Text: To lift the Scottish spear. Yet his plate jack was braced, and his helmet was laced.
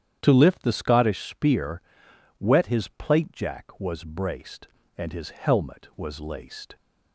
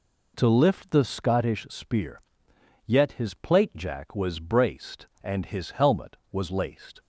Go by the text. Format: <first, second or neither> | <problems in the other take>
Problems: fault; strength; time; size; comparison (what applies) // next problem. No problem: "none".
second | starts louder than the rest; strong; until 1.2 s; 9.5 dB // says "Wet" for "Yet"; at 2.4 s